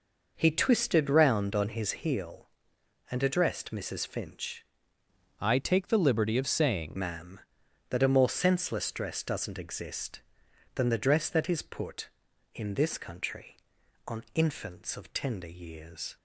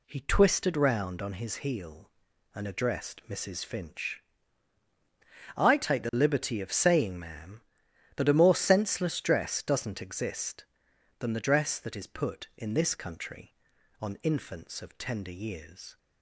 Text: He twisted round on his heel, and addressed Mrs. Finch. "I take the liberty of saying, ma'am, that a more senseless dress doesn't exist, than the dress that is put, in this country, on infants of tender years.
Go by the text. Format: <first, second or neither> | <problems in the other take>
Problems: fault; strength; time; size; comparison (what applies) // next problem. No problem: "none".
second | changes voice from "I" to "saying"; from 5.3 to 6.9 s; 1.6 s long